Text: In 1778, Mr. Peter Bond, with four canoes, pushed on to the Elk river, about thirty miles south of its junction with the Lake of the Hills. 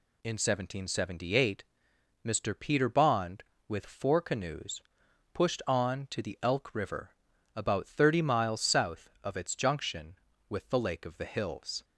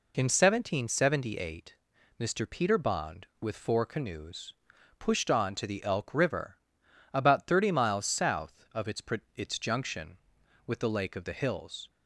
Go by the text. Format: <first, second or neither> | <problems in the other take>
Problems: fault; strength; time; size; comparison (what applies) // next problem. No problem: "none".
first | says "its" twice; at 9.3 s